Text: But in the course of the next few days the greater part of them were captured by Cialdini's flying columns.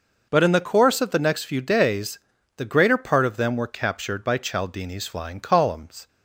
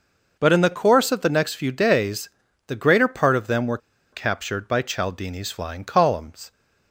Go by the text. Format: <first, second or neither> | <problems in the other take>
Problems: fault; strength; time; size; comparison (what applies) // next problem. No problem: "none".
first | pauses between "days" and "the"; at 2.2 s; 0.38 s long; also in the first // pauses between "were" and "captured"; slight; at 3.7 s; 0.34 s long